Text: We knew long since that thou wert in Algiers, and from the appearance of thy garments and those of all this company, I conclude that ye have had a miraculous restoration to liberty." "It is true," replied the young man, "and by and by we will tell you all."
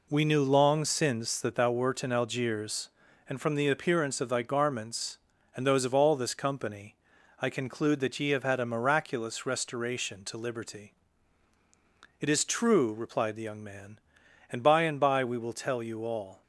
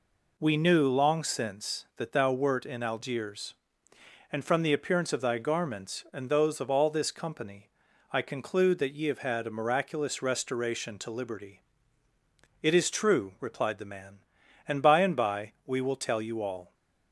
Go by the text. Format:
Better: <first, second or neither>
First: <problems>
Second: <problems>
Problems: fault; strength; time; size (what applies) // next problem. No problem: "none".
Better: first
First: none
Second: skips "young"; at 13.8 s